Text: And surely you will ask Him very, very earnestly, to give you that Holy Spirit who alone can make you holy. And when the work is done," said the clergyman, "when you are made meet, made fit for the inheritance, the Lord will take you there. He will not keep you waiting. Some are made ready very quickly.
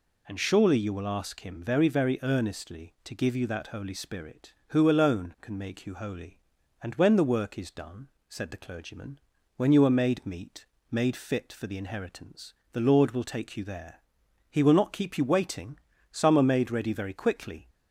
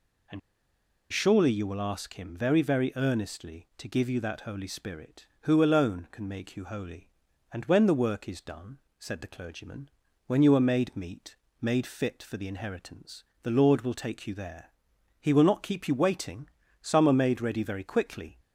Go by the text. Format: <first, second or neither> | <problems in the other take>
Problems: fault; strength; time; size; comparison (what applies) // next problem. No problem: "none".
first | pauses between "And" and "surely"; noticeable; at 0.3 s; 0.71 s long